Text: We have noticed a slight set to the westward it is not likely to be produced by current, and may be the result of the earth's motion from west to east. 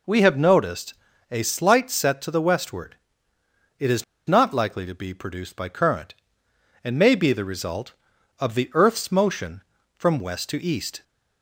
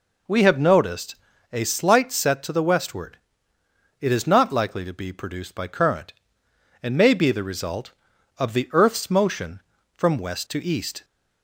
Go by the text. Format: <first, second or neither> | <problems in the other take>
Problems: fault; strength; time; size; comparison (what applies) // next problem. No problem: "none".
second | pauses between "noticed" and "a"; slight; at 0.9 s; 0.36 s long; slight in the second // pauses between "westward" and "it"; noticeable; at 2.9 s; 0.82 s long; noticeable in the second // pauses between "is" and "not"; slight; at 4.0 s; 0.22 s long